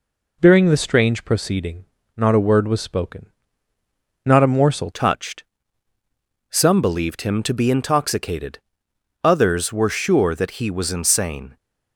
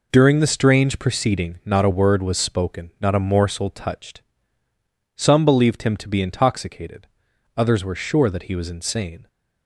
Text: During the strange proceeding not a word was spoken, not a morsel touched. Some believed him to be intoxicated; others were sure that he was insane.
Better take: second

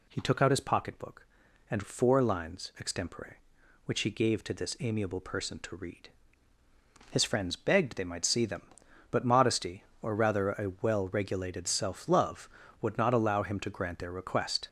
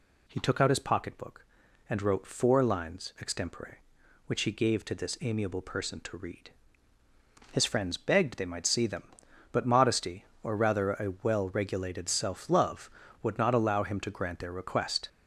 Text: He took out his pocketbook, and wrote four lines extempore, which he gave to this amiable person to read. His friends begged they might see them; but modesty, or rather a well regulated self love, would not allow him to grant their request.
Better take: second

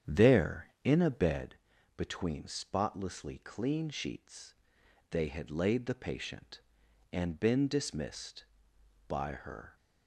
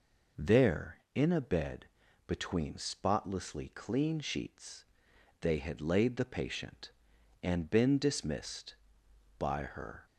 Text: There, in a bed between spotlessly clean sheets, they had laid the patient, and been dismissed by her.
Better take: second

